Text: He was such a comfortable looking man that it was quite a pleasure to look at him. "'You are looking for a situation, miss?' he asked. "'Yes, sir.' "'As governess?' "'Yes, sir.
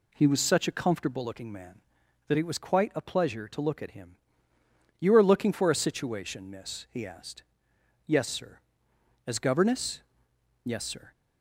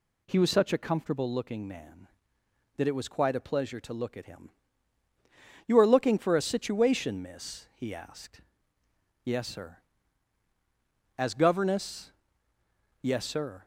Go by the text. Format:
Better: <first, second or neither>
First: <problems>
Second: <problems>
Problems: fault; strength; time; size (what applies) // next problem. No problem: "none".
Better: neither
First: none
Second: none